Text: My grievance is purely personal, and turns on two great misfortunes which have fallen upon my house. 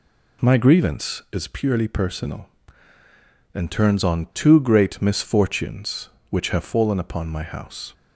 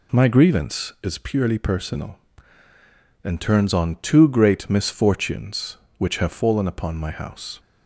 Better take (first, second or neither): neither